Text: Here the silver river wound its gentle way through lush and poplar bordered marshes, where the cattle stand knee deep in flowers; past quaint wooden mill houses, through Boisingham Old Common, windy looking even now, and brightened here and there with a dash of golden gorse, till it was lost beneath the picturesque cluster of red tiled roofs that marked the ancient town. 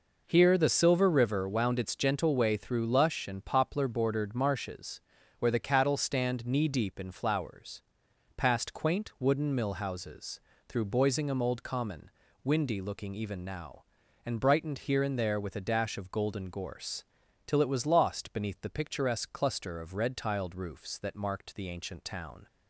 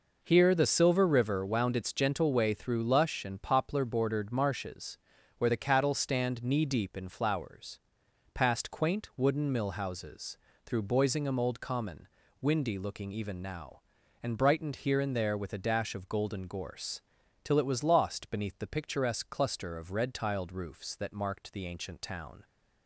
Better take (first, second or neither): neither